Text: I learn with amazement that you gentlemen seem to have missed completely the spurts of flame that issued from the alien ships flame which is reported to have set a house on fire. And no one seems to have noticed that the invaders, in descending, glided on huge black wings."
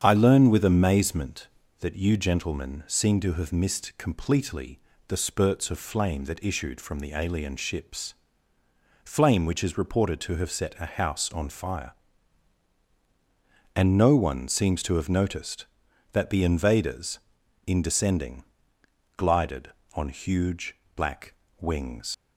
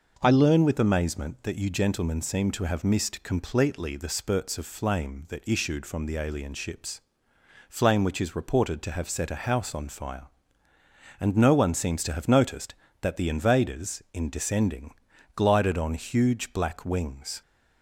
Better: second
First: starts louder than the rest; strong; until 1.0 s; 8 dB // pauses between "completely" and "the"; slight; at 4.8 s; 0.26 s long // pauses between "ships" and "flame"; noticeable; at 8.1 s; 0.90 s long // pauses between "huge" and "black"; slight; at 20.7 s; 0.20 s long // pauses between "black" and "wings"; slight; at 21.3 s; 0.26 s long // leaves "wings" unfinished; at 22.1 s; 75 ms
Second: pauses between "ships" and "flame"; noticeable; at 7.0 s; 0.68 s long

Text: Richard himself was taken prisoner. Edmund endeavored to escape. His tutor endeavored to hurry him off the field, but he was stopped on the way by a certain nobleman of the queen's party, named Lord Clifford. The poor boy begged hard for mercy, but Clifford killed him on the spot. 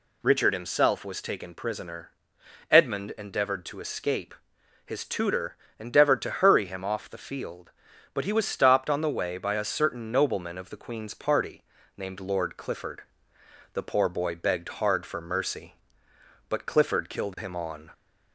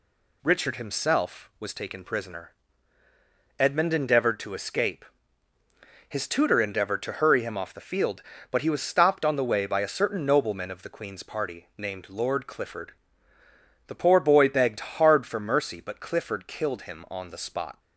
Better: second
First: pauses between "tutor" and "endeavored"; slight; at 5.5 s; 0.24 s long // stops before "the spot"; at 17.9 s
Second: none

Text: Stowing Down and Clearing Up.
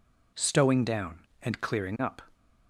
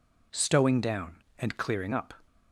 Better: neither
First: none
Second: none

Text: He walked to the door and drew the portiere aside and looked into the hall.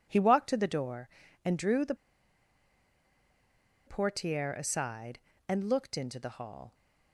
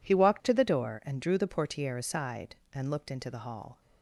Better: second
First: pauses between "the" and "portiere"; strong; at 1.9 s; 1.9 s long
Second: none

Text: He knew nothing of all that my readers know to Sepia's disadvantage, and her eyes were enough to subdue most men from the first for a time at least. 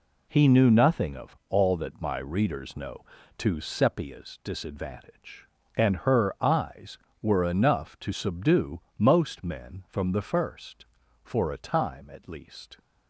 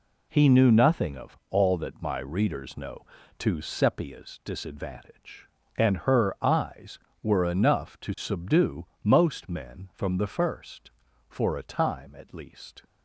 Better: neither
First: pauses between "subdue" and "most"; slight; at 8.8 s; 0.16 s long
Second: pauses between "subdue" and "most"; slight; at 8.8 s; 0.16 s long

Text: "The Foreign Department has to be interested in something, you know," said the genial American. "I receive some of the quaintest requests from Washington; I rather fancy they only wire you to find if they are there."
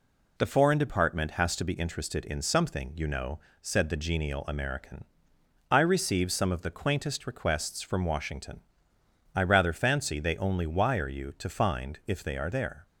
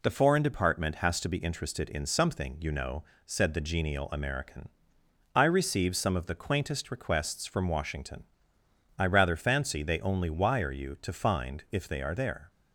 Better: neither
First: none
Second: none

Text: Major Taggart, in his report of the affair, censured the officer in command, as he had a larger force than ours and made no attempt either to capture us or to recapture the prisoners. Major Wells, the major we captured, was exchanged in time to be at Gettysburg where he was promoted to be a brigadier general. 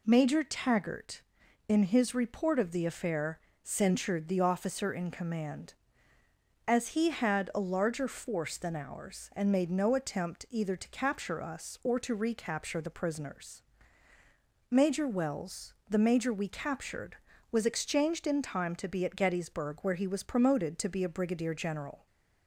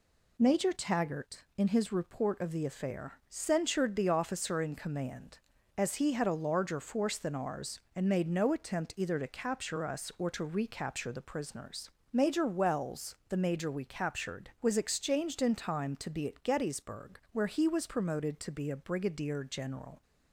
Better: neither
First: none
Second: none

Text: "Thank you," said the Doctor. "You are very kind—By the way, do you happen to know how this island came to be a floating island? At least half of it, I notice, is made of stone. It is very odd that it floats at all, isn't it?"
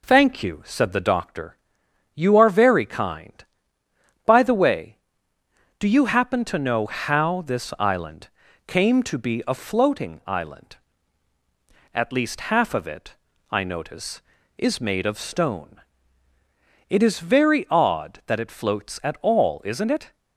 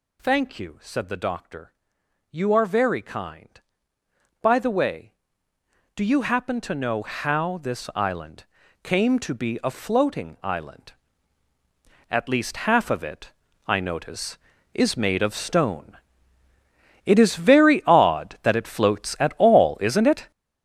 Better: first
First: pauses between "island" and "came"; at 8.2 s; 0.38 s long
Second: gets louder; strong; throughout; 8.5 dB // pauses between "island" and "came"; at 8.4 s; 0.38 s long

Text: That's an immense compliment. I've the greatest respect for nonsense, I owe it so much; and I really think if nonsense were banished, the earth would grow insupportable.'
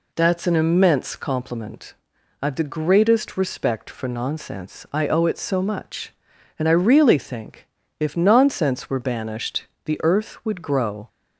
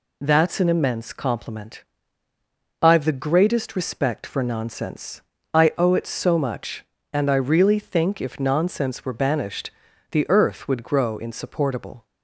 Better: second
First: pauses between "think" and "if"; slight; at 7.6 s; 0.32 s long // stops before "insupportable"; at 11.0 s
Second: none

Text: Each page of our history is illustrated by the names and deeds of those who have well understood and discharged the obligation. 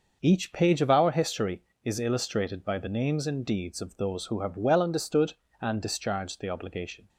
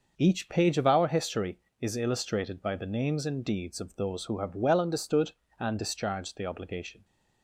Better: neither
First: starts louder than the rest; noticeable; until 1.2 s; 6 dB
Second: starts louder than the rest; noticeable; until 1.1 s; 6 dB

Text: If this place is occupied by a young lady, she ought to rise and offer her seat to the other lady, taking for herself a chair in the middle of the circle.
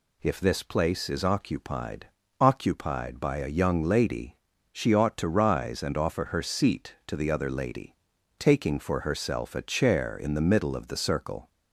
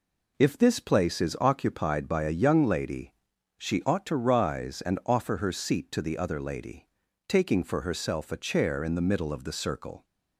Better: second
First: says "occupied" twice; at 2.3 s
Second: none

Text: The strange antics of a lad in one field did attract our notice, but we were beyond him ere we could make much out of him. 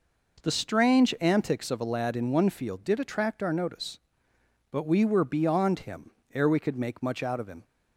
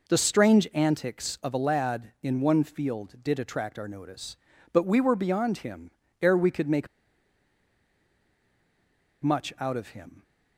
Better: first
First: pauses between "him" and "ere"; slight; at 6.1 s; 0.22 s long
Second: pauses between "him" and "ere"; slight; at 5.9 s; 0.30 s long // pauses between "make" and "much"; strong; at 6.8 s; 2.3 s long

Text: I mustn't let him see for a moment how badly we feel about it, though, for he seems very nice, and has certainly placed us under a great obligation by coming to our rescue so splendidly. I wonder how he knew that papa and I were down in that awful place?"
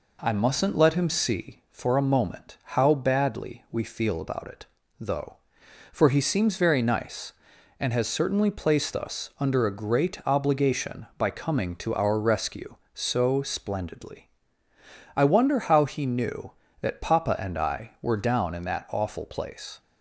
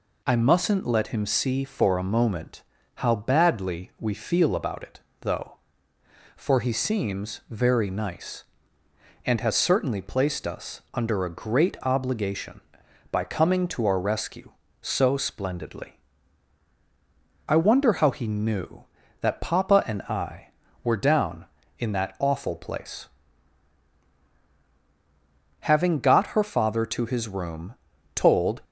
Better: first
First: none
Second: pauses between "moment" and "how"; slight; at 2.6 s; 0.32 s long // goes on to say "Having got her father to his room told"; strong; from 25.6 s on; 3.0 s long

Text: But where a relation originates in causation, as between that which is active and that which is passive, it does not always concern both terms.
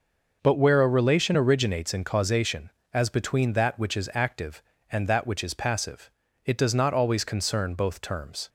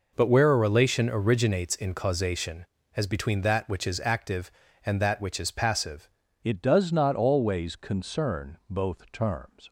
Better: first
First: none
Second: changes voice at "it"; from 6.4 s on; 3.2 s long

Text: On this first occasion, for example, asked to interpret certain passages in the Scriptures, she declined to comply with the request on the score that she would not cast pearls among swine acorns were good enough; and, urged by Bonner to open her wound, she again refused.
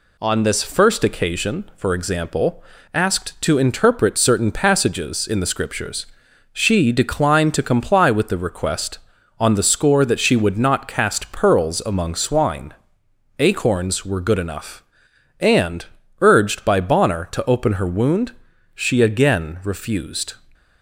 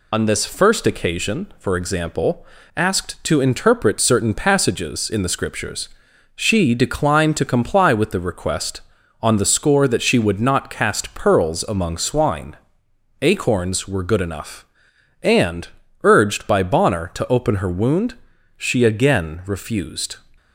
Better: first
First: pauses between "swine" and "acorns"; noticeable; at 12.7 s; 0.66 s long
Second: loses the start of "On"; at 0.1 s; 110 ms // pauses between "swine" and "acorns"; noticeable; at 12.5 s; 0.66 s long

